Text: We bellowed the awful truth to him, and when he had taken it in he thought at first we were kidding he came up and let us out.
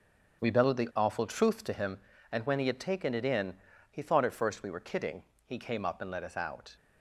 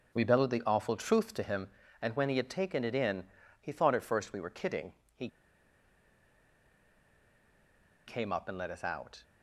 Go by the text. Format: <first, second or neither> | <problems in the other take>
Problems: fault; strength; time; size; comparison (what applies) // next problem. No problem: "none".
first | pauses between "in" and "he"; slight; at 3.2 s; 0.34 s long; slight in the first // pauses between "kidding" and "he"; slight; at 4.9 s; 0.22 s long; slight in the first // pauses between "he" and "came"; strong; at 5.2 s; 2.7 s long